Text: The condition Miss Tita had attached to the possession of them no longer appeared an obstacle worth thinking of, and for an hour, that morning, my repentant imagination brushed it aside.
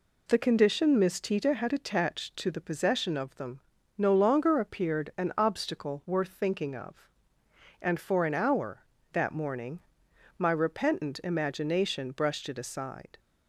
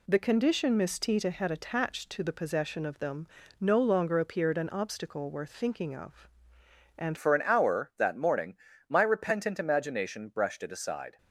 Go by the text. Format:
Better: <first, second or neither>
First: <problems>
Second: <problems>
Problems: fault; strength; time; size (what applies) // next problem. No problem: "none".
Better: first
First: pauses between "them" and "no"; slight; at 3.6 s; 0.36 s long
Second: pauses between "them" and "no"; slight; at 3.2 s; 0.32 s long // changes voice at "for"; from 7.1 s on; 4.0 s long